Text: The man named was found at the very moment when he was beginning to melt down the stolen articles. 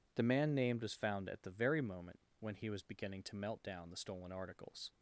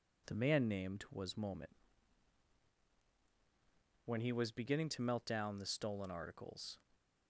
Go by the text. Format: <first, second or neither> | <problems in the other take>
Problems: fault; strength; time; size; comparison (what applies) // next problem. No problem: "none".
first | skips "found at the very"; at 1.3 s // pauses between "moment" and "when"; strong; at 1.7 s; 2.3 s long; slight in the first